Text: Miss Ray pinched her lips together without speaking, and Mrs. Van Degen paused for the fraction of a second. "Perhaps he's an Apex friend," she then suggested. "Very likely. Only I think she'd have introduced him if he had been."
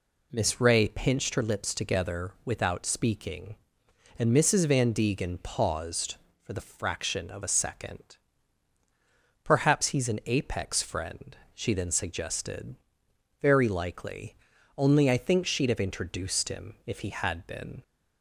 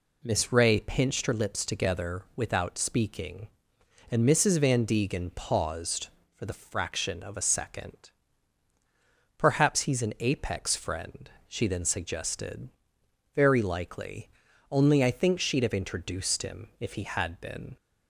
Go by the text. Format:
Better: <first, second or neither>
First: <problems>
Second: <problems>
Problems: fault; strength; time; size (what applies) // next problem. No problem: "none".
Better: neither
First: none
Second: none